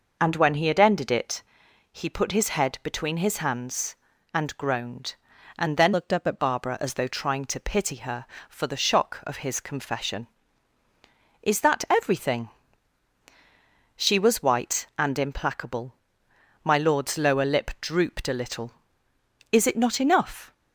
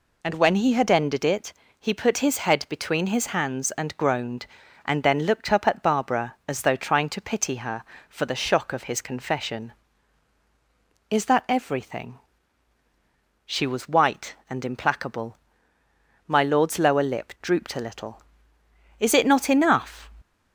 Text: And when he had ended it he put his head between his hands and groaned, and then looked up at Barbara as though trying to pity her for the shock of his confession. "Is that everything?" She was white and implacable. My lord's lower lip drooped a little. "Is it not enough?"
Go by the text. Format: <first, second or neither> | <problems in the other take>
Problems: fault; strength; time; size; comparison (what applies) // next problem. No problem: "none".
second | pauses between "it" and "he"; noticeable; at 1.4 s; 0.50 s long; slight in the second // changes voice from "looked" to "at"; from 5.9 to 6.3 s; 0.4 s long